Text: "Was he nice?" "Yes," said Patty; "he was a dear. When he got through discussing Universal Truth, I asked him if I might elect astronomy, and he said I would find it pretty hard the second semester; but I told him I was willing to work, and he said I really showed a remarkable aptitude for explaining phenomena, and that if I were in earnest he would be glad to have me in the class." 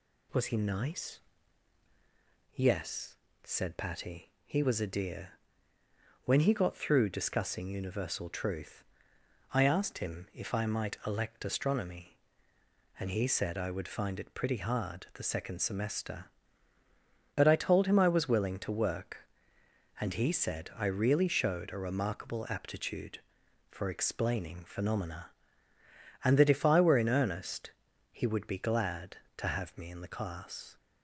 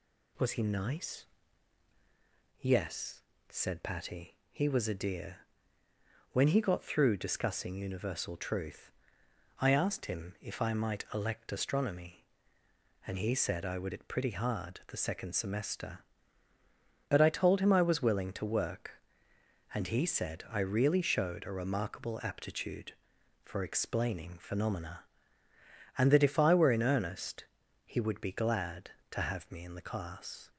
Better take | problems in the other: first | skips "find"; at 13.9 s // pauses between "earnest" and "he"; at 27.4 s; 0.40 s long; also in the first

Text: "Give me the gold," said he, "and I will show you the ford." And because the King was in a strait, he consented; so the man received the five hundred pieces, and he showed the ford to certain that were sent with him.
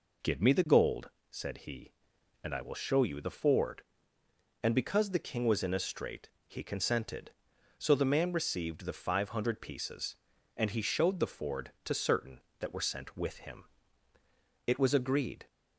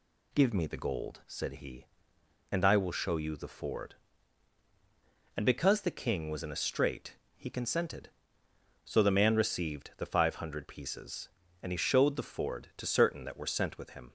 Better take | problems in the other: second | goes on to say "It was agreed"; noticeable; from 14.6 s on; 0.78 s long

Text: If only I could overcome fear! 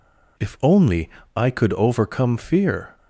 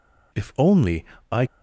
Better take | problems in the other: first | pauses between "only" and "I"; slight; at 1.0 s; 0.26 s long; slight in the first // stops before "could overcome fear"; at 1.4 s

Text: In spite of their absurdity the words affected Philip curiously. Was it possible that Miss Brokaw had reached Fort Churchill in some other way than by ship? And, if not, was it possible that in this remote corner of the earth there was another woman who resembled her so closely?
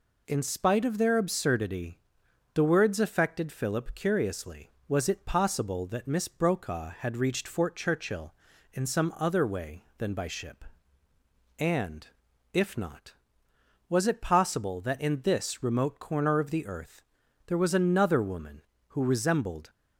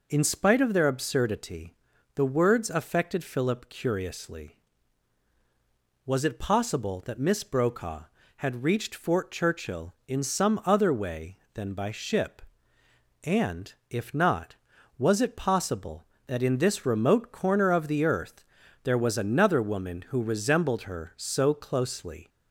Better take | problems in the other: second | pauses between "absurdity" and "the"; noticeable; at 1.9 s; 0.56 s long; also in the second // pauses between "earth" and "there"; noticeable; at 17.0 s; 0.46 s long; also in the second // stops before "her so closely"; at 19.6 s

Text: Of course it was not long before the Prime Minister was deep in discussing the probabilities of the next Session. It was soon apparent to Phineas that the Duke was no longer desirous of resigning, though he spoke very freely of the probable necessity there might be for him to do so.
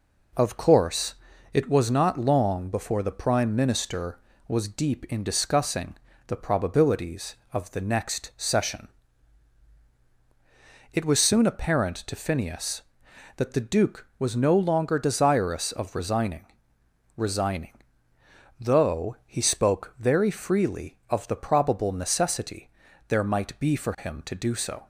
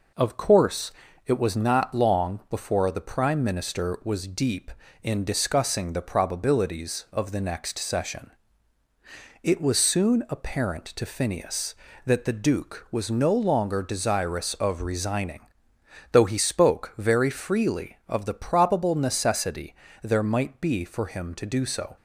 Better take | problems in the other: second | pauses between "course" and "it"; at 1.1 s; 0.38 s long; slight in the second // pauses between "discussing" and "the"; slight; at 5.9 s; 0.30 s long // says "resigning" twice; at 17.1 s // pauses between "necessity" and "there"; slight; at 22.6 s; 0.36 s long; slight in the second

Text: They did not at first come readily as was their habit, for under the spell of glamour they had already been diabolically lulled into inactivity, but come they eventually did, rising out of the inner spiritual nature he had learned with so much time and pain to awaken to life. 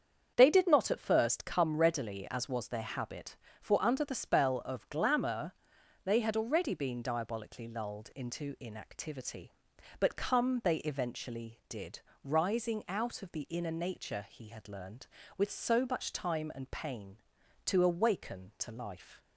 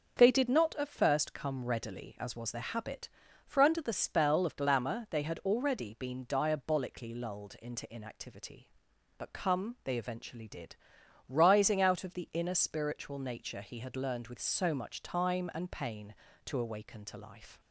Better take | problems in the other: second | starts louder than the rest; strong; until 1.3 s; 7.5 dB; also in the second // pauses between "glamour" and "they"; noticeable; at 5.5 s; 0.54 s long // skips "spiritual"; at 13.7 s

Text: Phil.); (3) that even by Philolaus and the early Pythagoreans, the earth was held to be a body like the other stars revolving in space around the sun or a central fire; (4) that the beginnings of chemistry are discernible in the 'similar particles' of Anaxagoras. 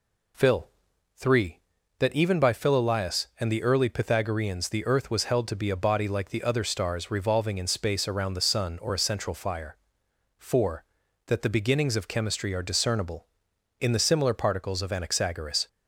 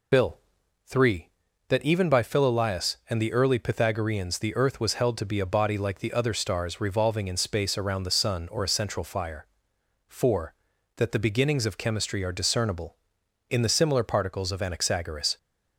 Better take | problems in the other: first | loses the start of "Phil"; at 0.1 s; 70 ms

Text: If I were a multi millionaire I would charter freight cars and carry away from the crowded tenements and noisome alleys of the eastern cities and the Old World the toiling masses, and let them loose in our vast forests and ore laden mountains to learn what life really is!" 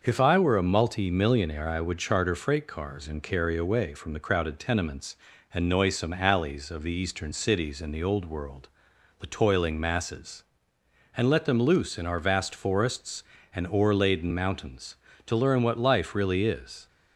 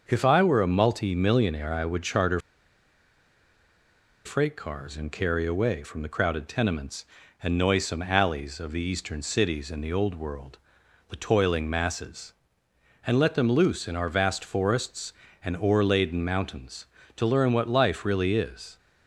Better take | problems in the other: first | starts louder than the rest; noticeable; until 1.0 s; 6 dB; noticeable in the first // pauses between "charter" and "freight"; strong; at 2.3 s; 1.8 s long // pauses between "World" and "the"; noticeable; at 10.5 s; 0.52 s long; noticeable in the first

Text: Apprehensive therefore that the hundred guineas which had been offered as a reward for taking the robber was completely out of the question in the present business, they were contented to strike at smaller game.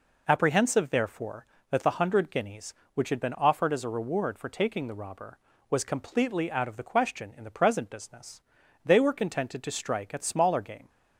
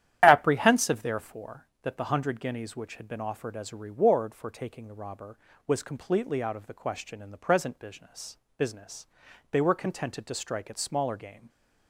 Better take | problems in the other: first | starts louder than the rest; strong; until 1.2 s; 11 dB // says "business" twice; at 8.5 s

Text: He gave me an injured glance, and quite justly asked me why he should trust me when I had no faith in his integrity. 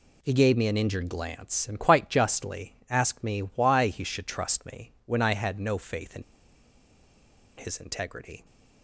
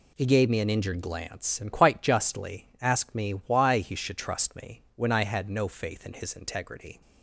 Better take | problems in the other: second | pauses between "in" and "his"; strong; at 6.2 s; 1.3 s long

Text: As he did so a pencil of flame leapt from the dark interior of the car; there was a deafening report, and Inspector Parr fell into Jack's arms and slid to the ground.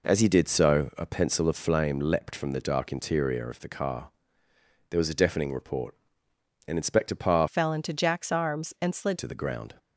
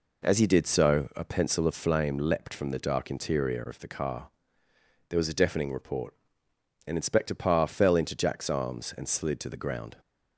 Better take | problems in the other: second | changes voice from "fell" to "slid"; from 7.4 to 9.1 s; 1.7 s long

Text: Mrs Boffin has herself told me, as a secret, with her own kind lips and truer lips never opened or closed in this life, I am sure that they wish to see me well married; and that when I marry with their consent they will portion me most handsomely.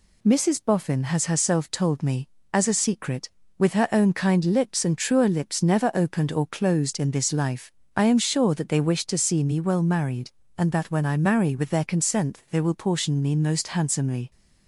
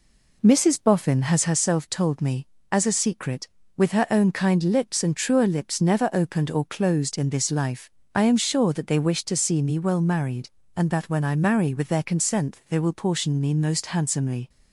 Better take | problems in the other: first | starts louder than the rest; slight; until 1.5 s; 3 dB

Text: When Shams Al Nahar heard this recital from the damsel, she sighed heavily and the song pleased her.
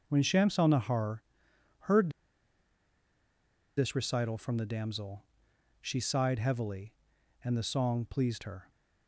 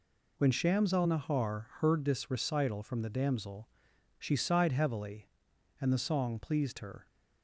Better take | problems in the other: second | pauses between "Nahar" and "heard"; noticeable; at 1.2 s; 0.58 s long // pauses between "heard" and "this"; strong; at 2.1 s; 1.6 s long

